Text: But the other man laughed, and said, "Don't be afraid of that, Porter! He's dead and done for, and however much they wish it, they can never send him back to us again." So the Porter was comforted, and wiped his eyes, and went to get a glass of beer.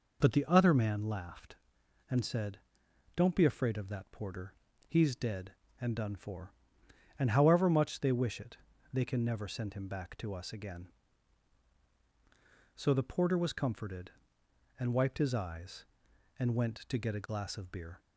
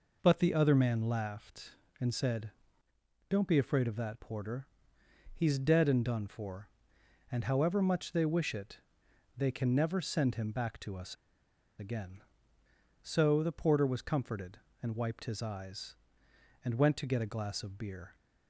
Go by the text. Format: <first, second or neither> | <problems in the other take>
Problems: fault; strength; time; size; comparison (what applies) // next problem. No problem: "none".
first | pauses between "us" and "again"; noticeable; at 11.1 s; 0.63 s long